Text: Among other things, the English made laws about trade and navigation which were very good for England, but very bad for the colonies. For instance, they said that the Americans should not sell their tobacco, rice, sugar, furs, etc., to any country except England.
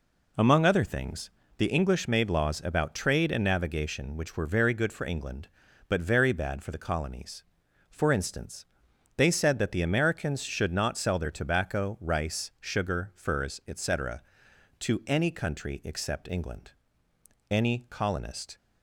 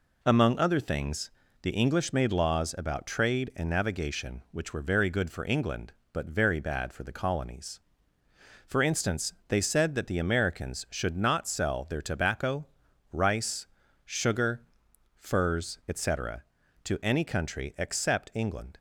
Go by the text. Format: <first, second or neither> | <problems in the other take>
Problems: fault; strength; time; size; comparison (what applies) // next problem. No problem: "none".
second | goes on to say "Any colonist"; noticeable; from 17.5 s on; 1.0 s long